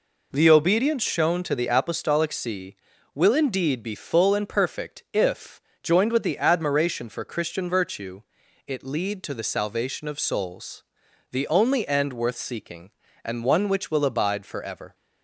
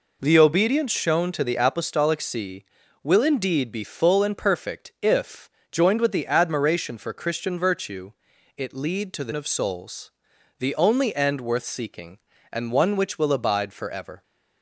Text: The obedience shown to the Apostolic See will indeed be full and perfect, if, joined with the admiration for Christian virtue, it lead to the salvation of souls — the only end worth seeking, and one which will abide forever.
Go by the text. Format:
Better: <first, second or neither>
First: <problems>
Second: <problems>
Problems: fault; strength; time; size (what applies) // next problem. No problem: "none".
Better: first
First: none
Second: skips "salvation"; at 9.3 s